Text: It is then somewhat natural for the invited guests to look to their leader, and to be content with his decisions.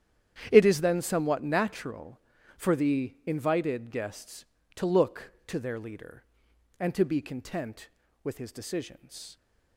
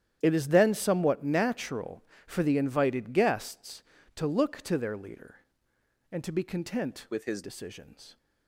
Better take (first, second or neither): first